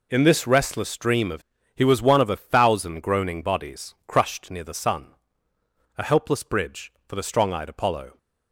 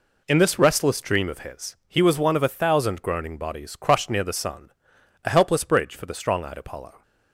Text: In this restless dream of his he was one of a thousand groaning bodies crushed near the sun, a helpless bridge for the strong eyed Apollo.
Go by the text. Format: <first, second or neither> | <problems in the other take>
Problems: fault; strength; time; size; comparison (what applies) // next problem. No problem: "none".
second | skips "his"; at 1.5 s